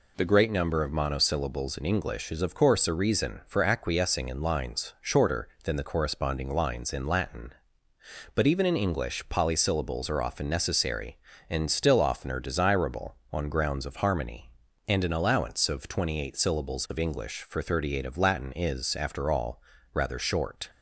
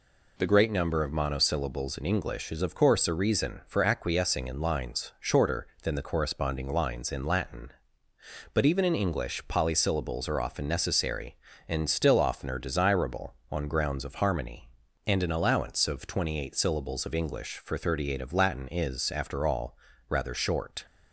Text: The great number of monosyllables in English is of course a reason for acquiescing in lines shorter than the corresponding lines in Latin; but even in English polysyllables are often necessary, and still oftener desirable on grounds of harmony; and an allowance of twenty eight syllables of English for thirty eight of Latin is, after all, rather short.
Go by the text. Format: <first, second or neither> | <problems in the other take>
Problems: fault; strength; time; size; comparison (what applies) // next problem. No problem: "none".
neither | none